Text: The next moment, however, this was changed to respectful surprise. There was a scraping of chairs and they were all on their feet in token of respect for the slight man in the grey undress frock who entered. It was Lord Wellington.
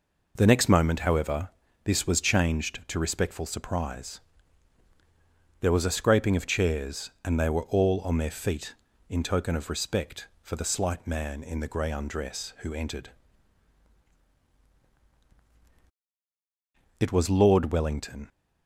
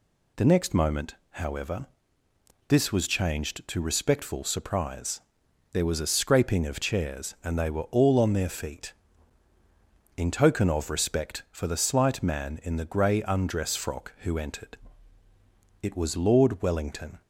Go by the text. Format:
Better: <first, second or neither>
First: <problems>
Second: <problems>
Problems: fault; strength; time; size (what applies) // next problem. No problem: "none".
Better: second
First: skips "frock"; at 12.5 s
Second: none